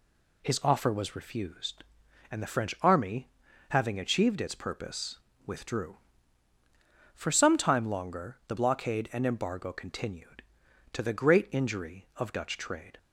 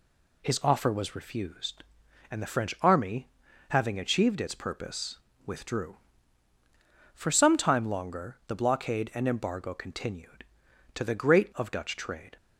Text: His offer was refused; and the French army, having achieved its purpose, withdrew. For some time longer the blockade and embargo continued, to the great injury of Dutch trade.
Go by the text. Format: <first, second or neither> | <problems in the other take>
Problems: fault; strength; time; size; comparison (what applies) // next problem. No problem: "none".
first | skips "injury"; at 11.5 s